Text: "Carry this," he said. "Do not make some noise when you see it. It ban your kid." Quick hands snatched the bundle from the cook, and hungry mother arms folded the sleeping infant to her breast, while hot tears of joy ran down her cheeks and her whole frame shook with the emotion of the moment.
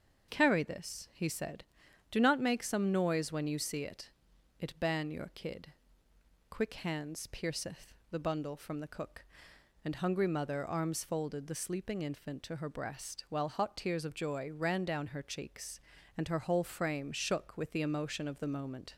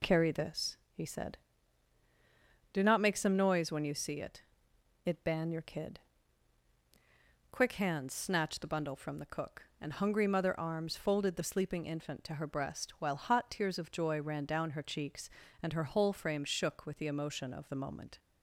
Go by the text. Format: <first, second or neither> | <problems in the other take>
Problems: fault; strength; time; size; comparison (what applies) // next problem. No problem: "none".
second | starts louder than the rest; until 1.3 s; 6.5 dB // says "pierceth" for "snatched"; at 7.2 s